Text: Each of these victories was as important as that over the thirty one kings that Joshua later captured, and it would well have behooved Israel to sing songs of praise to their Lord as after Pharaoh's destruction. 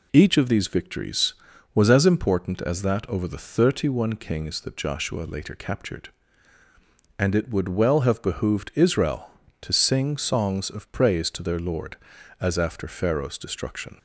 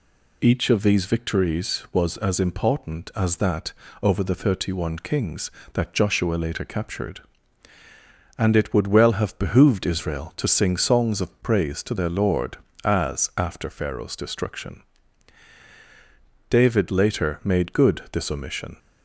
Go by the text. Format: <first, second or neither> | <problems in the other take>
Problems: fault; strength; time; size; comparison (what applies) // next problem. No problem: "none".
first | pauses between "that" and "over"; slight; at 3.7 s; 0.30 s long // goes on to say "David later made good this omission"; strong; from 16.4 s on; 2.3 s long